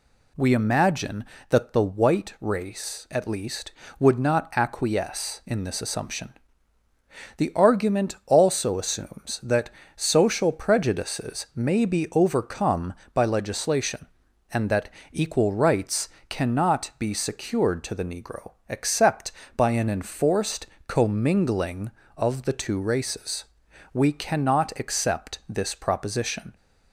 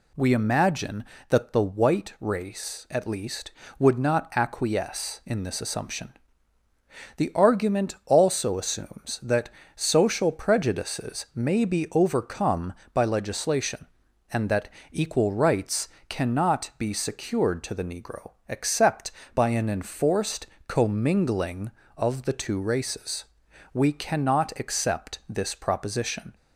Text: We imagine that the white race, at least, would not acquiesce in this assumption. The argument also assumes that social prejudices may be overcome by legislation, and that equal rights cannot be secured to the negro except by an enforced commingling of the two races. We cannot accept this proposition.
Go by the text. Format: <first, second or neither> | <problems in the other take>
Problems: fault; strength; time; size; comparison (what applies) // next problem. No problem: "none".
neither | pauses between "that" and "social"; slight; the same in both // pauses between "that" and "equal"; slight; the same in both // pauses between "rights" and "cannot"; slight; the same in both // pauses between "negro" and "except"; slight; the same in both // pauses between "enforced" and "commingling"; slight; the same in both